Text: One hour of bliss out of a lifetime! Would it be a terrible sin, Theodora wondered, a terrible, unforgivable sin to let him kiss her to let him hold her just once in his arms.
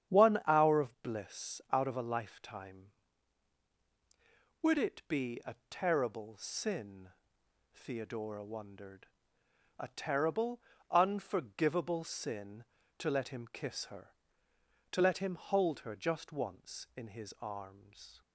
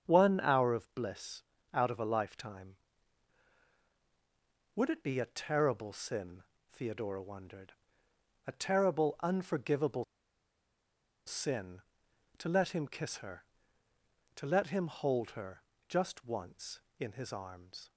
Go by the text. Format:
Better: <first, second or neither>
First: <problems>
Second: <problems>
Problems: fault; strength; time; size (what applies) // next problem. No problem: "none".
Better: first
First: starts louder than the rest; strong; until 1.1 s; 8.5 dB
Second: starts louder than the rest; strong; until 1.0 s; 7.5 dB // pauses between "bliss" and "out"; slight; at 1.4 s; 0.32 s long // pauses between "unforgivable" and "sin"; at 10.0 s; 1.2 s long // pauses between "her" and "just"; slight; at 15.6 s; 0.26 s long